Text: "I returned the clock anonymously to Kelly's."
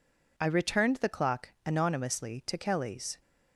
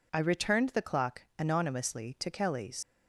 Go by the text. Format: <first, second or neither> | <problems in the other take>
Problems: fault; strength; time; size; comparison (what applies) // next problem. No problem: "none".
first | leaves "Kelly's" unfinished; at 2.8 s; 105 ms